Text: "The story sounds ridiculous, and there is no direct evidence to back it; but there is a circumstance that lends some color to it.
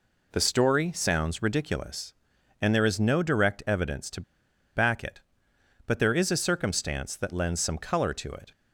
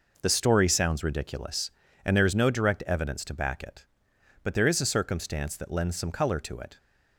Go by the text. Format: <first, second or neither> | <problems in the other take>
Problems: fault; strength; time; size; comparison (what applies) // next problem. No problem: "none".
second | pauses between "to" and "back"; noticeable; at 4.2 s; 0.53 s long